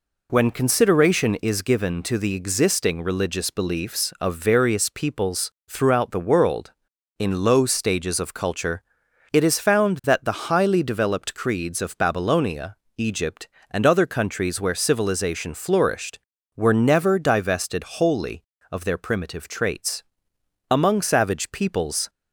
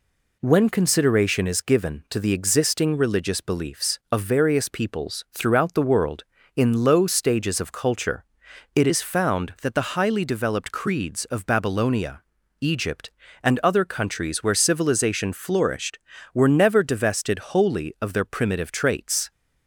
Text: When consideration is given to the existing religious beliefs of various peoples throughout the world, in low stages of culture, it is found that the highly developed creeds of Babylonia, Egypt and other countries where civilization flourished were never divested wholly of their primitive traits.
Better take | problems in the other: second | pauses between "peoples" and "throughout"; slight; at 5.5 s; 0.18 s long // goes on to say "Among savage peoples"; from 20.6 s on; 1.4 s long

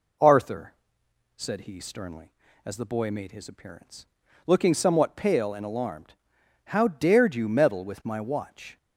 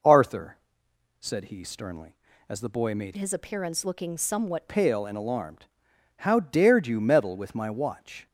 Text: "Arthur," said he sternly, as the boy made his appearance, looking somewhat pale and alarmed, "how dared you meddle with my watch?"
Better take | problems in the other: first | changes voice from "his" to "somewhat"; from 3.1 to 4.6 s; 1.5 s long

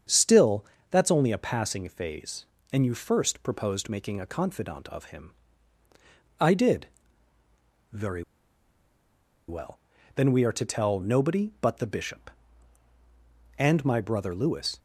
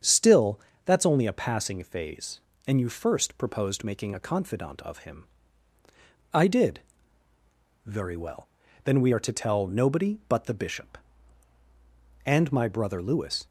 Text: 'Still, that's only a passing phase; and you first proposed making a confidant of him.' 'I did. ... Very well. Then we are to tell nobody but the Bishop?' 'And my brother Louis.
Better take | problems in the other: second | starts louder than the rest; strong; until 1.3 s; 7.5 dB; strong in the second // pauses between "Very" and "well"; at 8.2 s; 1.2 s long

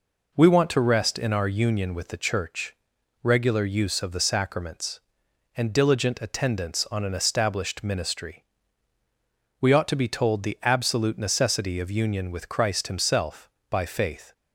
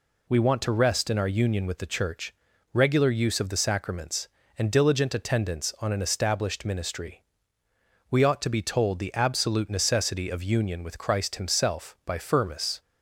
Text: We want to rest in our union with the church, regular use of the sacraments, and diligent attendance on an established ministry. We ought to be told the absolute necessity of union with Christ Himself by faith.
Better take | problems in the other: first | says "firmus" for "faith"; at 12.1 s

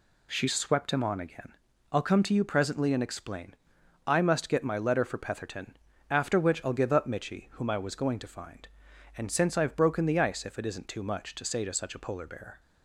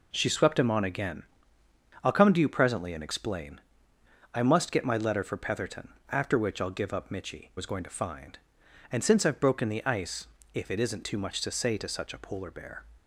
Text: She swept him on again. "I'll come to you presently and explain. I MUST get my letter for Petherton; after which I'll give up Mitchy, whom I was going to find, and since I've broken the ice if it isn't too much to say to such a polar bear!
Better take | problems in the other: first | skips "whom I"; at 7.5 s // pauses between "ice" and "if"; slight; at 10.2 s; 0.28 s long

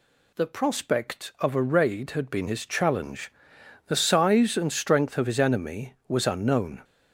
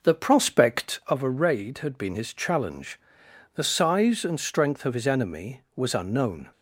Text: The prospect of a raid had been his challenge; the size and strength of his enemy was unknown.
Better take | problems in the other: first | starts louder than the rest; noticeable; until 1.2 s; 5 dB

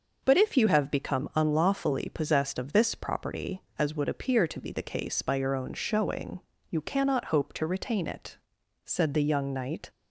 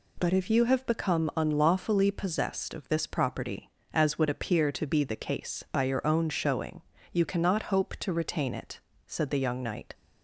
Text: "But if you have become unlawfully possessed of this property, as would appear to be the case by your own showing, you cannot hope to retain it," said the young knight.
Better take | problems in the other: neither | none

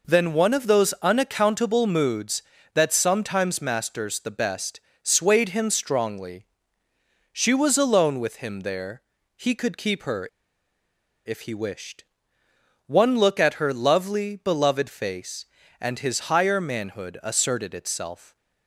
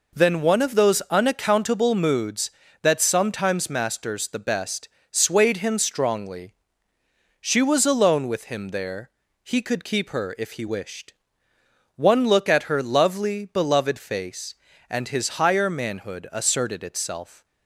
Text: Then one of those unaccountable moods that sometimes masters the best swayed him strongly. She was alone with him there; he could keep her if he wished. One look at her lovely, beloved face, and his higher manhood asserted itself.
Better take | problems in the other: second | pauses between "best" and "swayed"; slight; at 4.7 s; 0.22 s long; slight in the second // pauses between "her" and "if"; noticeable; at 10.2 s; 0.97 s long

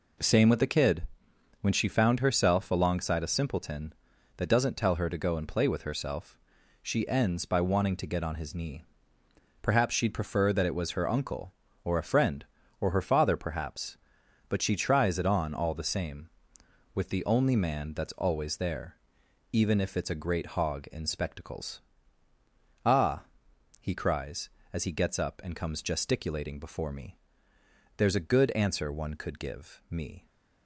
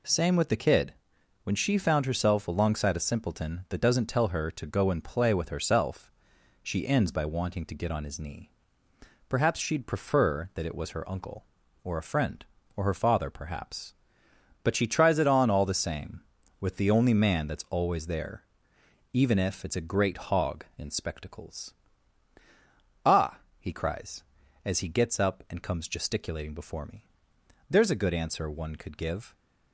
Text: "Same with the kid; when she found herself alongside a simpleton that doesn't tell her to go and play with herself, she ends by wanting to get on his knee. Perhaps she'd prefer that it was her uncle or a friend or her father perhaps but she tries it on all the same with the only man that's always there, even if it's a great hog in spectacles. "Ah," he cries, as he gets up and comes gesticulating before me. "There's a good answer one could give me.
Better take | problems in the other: first | stops before "me"; at 29.3 s

